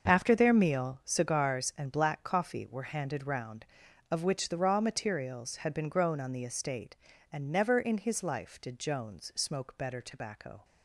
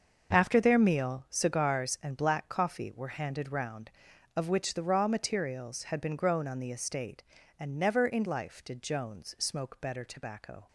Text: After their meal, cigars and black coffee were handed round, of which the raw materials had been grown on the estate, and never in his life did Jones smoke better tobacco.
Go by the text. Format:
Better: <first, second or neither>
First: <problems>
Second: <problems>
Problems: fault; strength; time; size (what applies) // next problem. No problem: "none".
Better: first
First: starts louder than the rest; until 1.1 s; 6.5 dB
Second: starts louder than the rest; until 1.3 s; 6.5 dB // skips "his"; at 8.2 s